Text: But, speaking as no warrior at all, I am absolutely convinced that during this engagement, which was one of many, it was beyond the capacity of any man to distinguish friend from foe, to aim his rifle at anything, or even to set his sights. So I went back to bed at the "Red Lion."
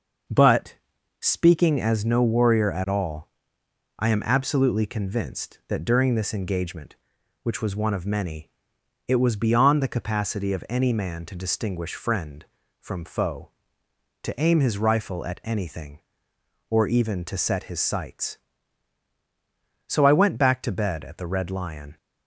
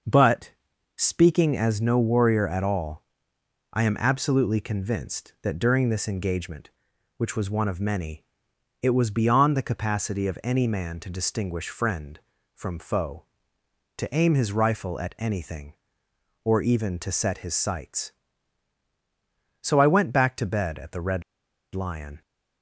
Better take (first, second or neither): first